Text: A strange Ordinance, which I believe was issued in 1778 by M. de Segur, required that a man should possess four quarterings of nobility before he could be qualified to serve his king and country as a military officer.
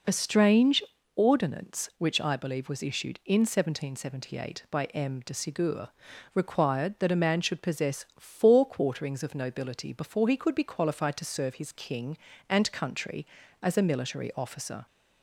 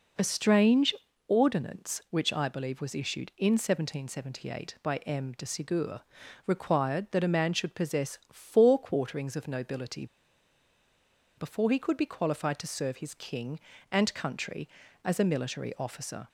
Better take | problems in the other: first | pauses between "strange" and "Ordinance"; slight; at 0.9 s; 0.34 s long; slight in the first // pauses between "nobility" and "before"; strong; at 10.0 s; 1.3 s long

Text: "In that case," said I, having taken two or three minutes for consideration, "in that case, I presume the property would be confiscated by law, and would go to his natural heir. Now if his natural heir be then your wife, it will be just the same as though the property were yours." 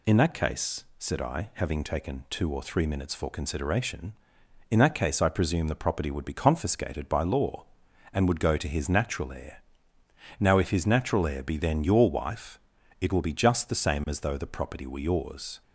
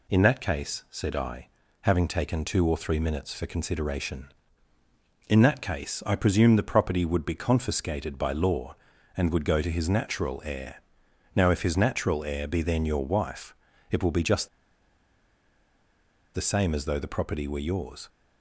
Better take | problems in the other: first | pauses between "just" and "the"; strong; at 14.4 s; 1.8 s long

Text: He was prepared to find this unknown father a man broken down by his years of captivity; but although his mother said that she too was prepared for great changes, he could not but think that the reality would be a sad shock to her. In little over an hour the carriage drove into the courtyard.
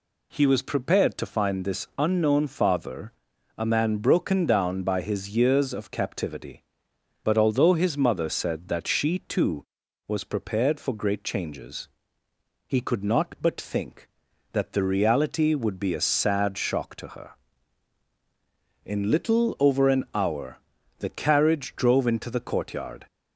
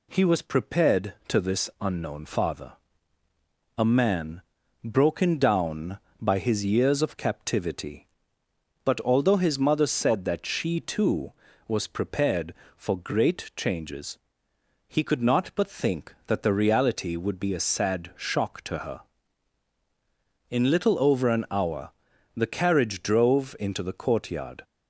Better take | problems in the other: first | skips "find"; at 1.3 s // pauses between "father" and "a"; at 2.7 s; 1.0 s long; noticeable in the first // pauses between "man" and "broken"; at 4.4 s; 0.42 s long // pauses between "hour" and "the"; at 21.9 s; 0.44 s long; also in the first

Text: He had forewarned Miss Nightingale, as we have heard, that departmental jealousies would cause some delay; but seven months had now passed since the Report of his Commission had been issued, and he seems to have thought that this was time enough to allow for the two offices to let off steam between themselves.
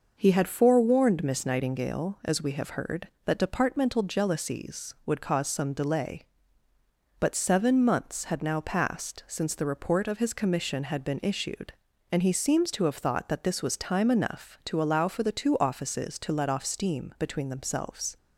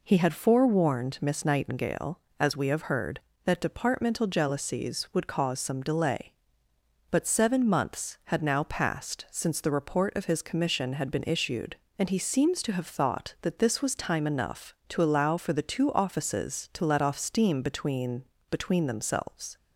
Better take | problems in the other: first | says "between" twice; at 18.4 s

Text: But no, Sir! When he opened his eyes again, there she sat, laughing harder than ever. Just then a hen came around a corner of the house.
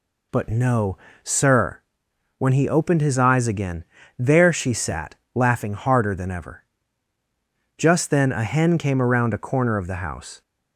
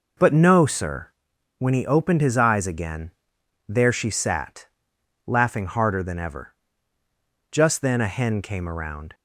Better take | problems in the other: first | stops before "a corner of the house"; at 9.1 s

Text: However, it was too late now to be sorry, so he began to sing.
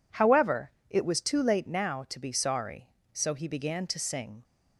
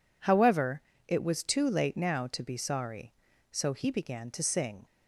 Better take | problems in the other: neither | none

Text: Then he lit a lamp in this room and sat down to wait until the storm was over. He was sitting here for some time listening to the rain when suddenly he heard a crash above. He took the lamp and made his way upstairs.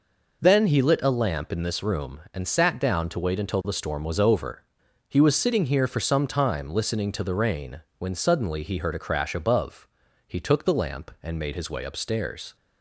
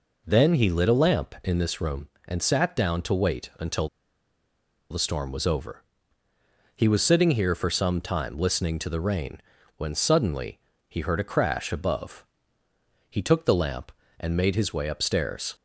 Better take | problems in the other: first | pauses between "until" and "the"; at 3.8 s; 1.0 s long // pauses between "rain" and "when"; at 9.3 s; 0.38 s long; slight in the first // pauses between "suddenly" and "he"; slight; at 10.5 s; 0.30 s long

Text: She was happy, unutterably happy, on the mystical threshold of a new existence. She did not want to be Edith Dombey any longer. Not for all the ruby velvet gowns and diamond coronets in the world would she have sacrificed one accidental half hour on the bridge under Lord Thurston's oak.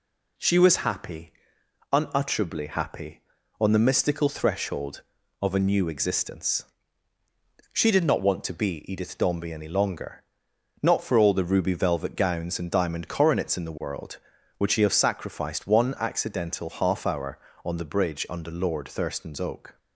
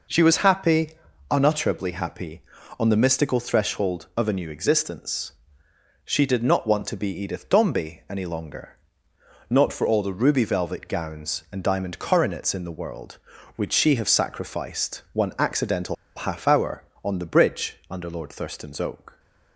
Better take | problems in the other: first | pauses between "accidental" and "half"; slight; at 15.9 s; 0.21 s long

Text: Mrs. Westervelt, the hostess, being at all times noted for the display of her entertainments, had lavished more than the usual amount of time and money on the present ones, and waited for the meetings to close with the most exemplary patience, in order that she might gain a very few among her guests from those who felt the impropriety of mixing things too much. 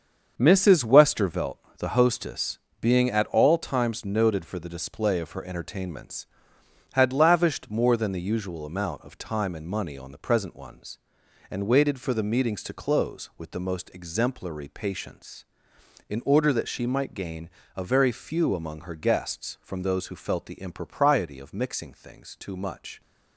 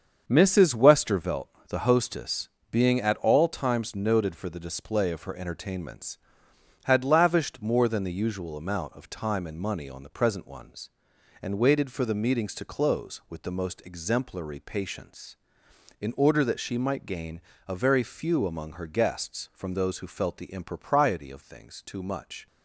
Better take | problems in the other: first | starts louder than the rest; until 1.2 s; 7 dB; also in the first // pauses between "gain" and "a"; slight; at 17.3 s; 0.28 s long; slight in the first // skips "mixing"; at 21.4 s

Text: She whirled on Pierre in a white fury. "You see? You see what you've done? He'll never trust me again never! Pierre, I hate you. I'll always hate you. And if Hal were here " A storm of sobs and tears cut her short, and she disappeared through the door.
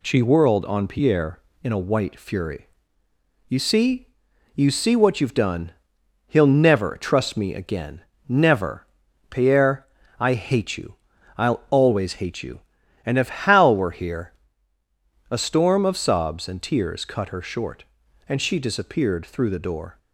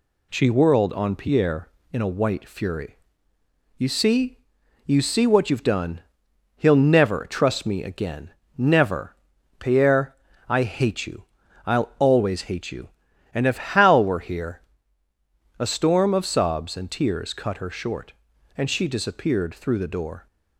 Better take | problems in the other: neither | pauses between "again" and "never"; slight; the same in both

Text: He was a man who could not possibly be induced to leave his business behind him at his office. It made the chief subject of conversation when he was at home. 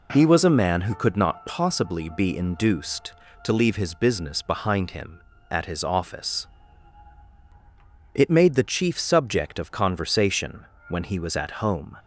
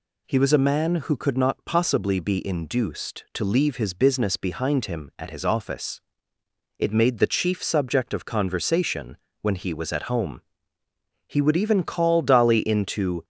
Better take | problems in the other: first | pauses between "conversation" and "when"; slight; at 9.1 s; 0.26 s long; slight in the first // goes on to say "He would even call Dolly into"; strong; from 11.2 s on; 1.9 s long

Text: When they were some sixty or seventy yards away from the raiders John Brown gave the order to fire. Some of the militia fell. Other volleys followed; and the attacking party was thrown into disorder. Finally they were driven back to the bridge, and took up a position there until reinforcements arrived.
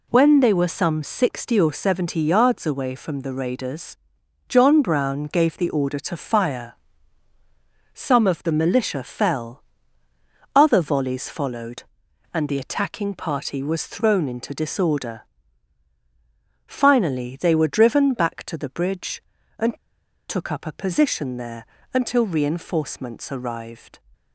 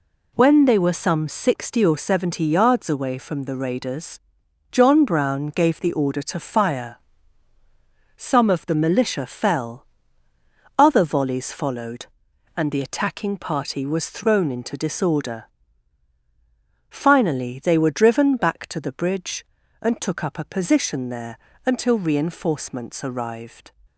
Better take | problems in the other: second | pauses between "raiders" and "John"; noticeable; at 3.9 s; 0.52 s long; noticeable in the second // pauses between "and" and "took"; noticeable; at 19.7 s; 0.53 s long // pauses between "there" and "until"; slight; at 21.6 s; 0.26 s long; slight in the second

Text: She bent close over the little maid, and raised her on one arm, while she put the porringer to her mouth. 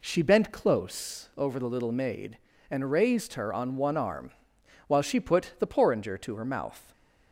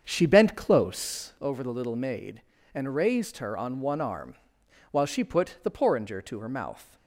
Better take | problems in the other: first | starts louder than the rest; strong; until 1.4 s; 7 dB

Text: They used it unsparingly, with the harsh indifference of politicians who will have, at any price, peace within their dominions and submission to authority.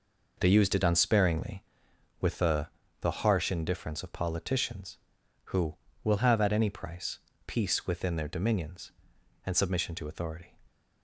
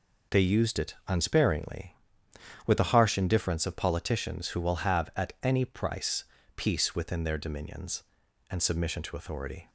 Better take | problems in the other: second | says "the" twice; at 3.0 s

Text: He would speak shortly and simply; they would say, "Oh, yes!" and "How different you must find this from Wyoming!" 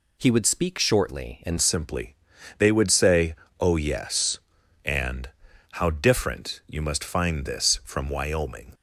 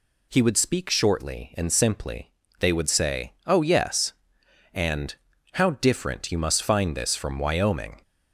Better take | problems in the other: second | changes voice at "simply"; from 1.5 s on; 7.2 s long // pauses between "and" and "How"; at 5.2 s; 0.42 s long; also in the second

